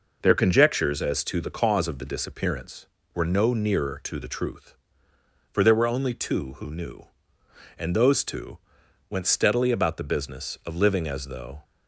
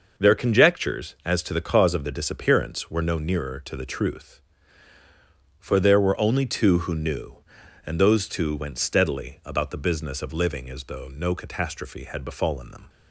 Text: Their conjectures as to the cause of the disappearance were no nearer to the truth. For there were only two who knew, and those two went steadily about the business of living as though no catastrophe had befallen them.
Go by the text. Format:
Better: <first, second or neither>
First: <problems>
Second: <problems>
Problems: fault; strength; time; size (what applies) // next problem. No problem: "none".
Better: second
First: pauses between "two" and "went"; noticeable; at 8.5 s; 0.50 s long // stops before "no catastrophe had befallen them"; at 11.6 s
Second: none